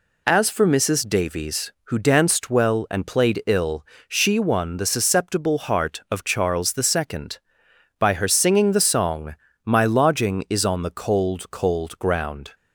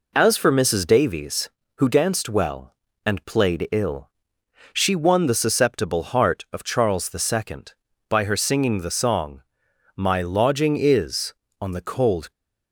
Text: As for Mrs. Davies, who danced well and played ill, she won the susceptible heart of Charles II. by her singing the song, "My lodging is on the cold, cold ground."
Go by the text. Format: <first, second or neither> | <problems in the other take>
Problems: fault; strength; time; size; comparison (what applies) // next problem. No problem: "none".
first | stops before "cold ground"; at 12.3 s